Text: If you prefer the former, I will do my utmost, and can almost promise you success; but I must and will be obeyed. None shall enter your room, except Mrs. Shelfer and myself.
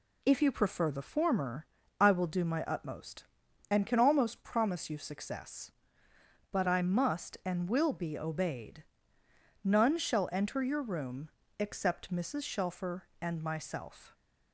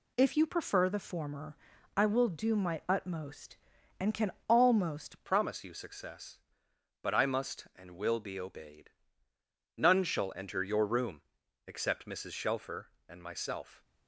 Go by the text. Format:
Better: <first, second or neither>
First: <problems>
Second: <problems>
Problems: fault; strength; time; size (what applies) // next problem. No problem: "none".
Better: first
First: none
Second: pauses between "can" and "almost"; slight; at 4.2 s; 0.18 s long // changes voice at "promise"; from 5.2 s on; 8.6 s long